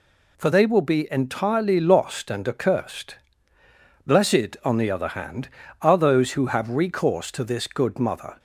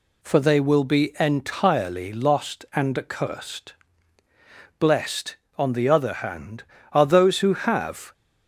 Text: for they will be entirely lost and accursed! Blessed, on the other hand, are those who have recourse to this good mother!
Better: first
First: none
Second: stops before "recourse to this good mother"; at 8.1 s

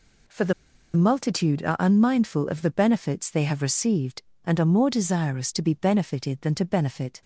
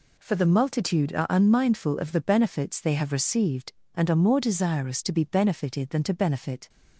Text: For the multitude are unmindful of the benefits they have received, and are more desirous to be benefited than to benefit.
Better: second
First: pauses between "the" and "multitude"; at 0.5 s; 0.42 s long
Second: none

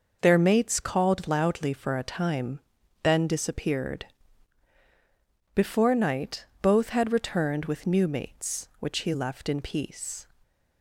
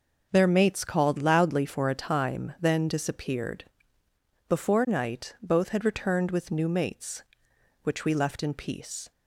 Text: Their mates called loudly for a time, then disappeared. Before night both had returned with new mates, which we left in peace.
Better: second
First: pauses between "night" and "both"; slight; at 6.4 s; 0.16 s long // says "he" for "we"; at 9.0 s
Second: none

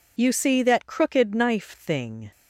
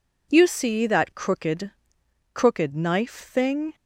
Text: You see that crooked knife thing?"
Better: first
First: none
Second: says "crooked" twice; at 2.3 s

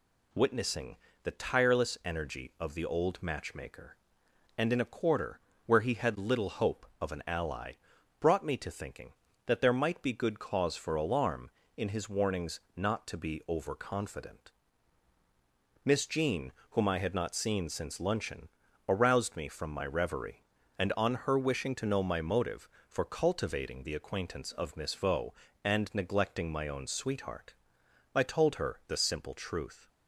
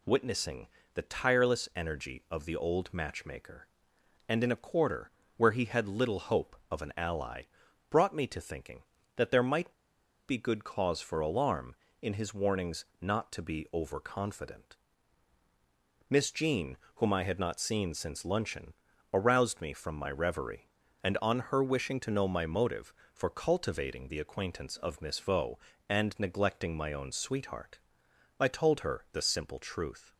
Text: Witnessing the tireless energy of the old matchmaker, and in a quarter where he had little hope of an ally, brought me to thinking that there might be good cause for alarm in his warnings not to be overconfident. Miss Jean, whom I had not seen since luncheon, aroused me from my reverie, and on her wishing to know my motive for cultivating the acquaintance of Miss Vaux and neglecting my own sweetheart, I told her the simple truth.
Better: first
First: pauses between "Witnessing" and "the"; slight; at 0.9 s; 0.28 s long // pauses between "quarter" and "where"; slight; at 5.4 s; 0.24 s long // pauses between "warnings" and "not"; slight; at 12.5 s; 0.18 s long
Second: pauses between "Witnessing" and "the"; slight; at 0.6 s; 0.28 s long // pauses between "quarter" and "where"; slight; at 5.1 s; 0.24 s long // pauses between "might" and "be"; noticeable; at 9.7 s; 0.55 s long // pauses between "warnings" and "not"; slight; at 12.8 s; 0.18 s long

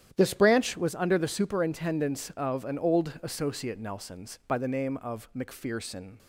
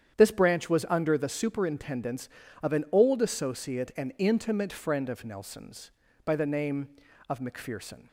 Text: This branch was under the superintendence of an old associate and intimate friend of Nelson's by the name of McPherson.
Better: second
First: starts louder than the rest; strong; until 1.1 s; 10.5 dB // skips "and intimate friend of"; at 3.7 s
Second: starts louder than the rest; strong; until 1.2 s; 9 dB

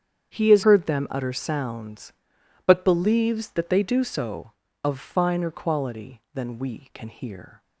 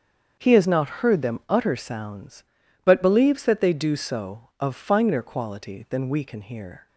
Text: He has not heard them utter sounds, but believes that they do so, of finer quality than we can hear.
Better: second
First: starts louder than the rest; strong; until 1.3 s; 8 dB // skips "not"; at 0.6 s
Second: starts louder than the rest; until 1.4 s; 7 dB

